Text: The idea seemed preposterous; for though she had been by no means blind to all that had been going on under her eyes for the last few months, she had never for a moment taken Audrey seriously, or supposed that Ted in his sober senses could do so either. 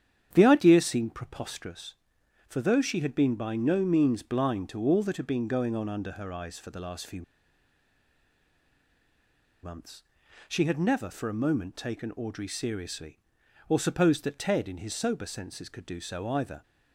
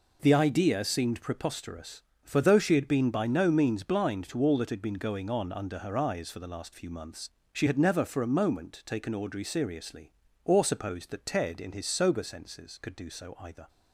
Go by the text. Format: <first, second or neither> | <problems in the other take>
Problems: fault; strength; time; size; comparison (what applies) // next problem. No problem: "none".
second | starts louder than the rest; strong; until 1.3 s; 9 dB // pauses between "few" and "months"; strong; at 7.2 s; 2.4 s long